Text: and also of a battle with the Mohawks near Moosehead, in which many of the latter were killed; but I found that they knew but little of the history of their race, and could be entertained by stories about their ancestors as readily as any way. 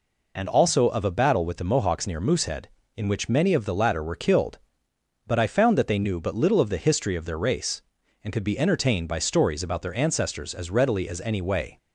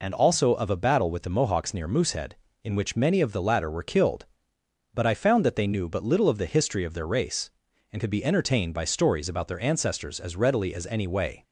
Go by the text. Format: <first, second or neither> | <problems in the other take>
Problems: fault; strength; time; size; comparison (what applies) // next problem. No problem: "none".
neither | none